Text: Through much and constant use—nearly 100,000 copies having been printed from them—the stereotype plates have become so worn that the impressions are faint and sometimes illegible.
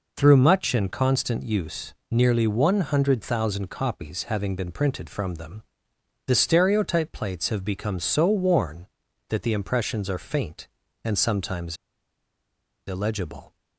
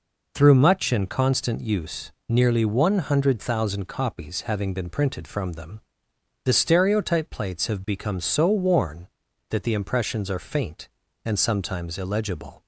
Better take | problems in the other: second | pauses between "sometimes" and "illegible"; at 11.7 s; 1.1 s long

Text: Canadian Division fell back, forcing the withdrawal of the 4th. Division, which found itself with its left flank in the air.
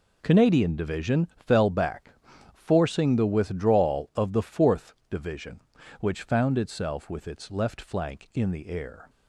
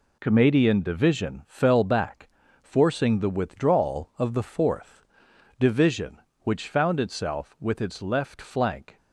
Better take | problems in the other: first | stops before "in the air"; at 8.9 s

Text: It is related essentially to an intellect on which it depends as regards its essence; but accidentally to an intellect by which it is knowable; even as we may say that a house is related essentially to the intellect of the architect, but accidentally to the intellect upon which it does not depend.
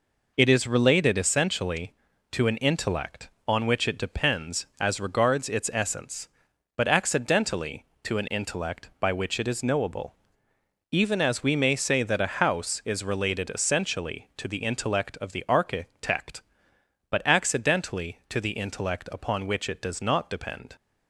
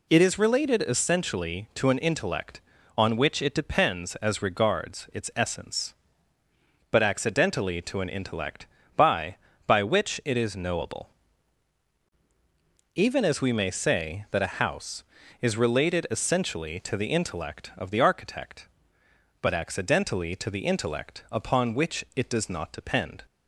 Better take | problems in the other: first | says "by" twice; at 9.6 s

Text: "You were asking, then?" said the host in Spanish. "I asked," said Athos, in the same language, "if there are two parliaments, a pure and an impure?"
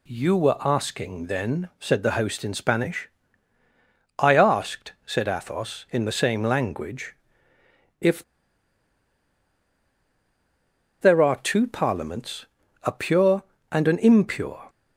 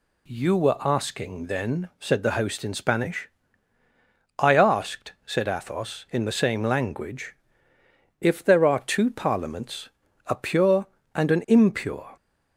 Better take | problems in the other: second | pauses between "if" and "there"; strong; at 8.2 s; 2.7 s long

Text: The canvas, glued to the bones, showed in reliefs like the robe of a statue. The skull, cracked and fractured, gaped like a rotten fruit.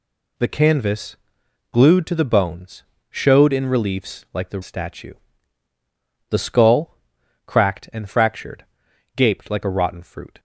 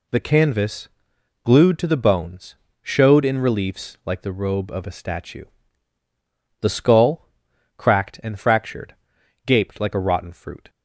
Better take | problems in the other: second | skips "robe of a"; at 4.6 s

